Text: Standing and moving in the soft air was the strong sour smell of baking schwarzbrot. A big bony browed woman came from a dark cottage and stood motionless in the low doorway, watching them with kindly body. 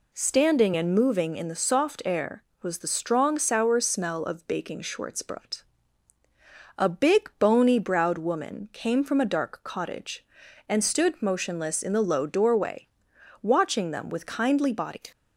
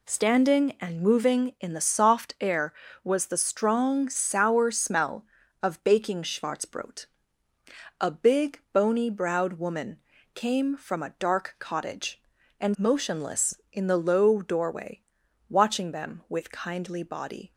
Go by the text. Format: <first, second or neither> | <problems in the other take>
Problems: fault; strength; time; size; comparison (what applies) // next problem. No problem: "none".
first | pauses between "woman" and "came"; slight; at 9.9 s; 0.34 s long // skips "stood"; at 12.7 s